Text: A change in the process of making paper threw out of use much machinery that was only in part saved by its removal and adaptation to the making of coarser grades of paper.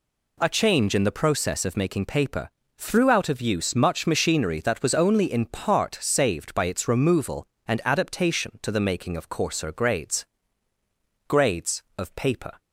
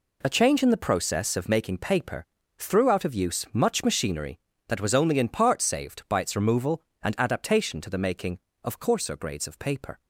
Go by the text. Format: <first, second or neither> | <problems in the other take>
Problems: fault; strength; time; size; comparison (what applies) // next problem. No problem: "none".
second | pauses between "paper" and "threw"; slight; at 2.4 s; 0.28 s long; slight in the second // says "grades" twice; at 11.2 s